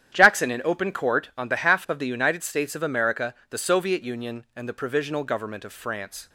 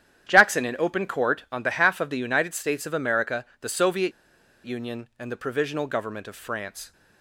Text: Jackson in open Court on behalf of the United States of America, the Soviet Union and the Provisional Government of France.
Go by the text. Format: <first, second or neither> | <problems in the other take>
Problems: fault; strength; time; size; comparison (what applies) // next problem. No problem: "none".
first | starts louder than the rest; strong; until 1.3 s; 10.5 dB; strong in the first // pauses between "Soviet" and "Union"; noticeable; at 4.1 s; 0.52 s long